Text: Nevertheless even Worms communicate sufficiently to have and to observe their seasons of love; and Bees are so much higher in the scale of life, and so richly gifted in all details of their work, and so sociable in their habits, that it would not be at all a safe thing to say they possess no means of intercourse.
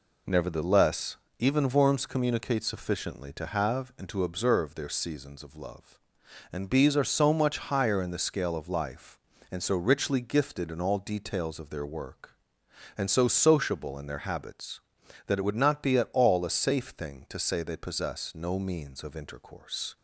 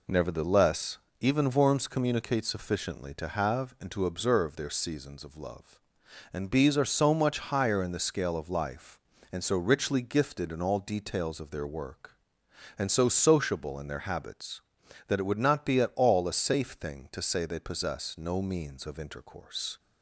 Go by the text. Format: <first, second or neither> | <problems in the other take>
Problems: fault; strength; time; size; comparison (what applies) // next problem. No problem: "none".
neither | pauses between "Nevertheless" and "even"; slight; the same in both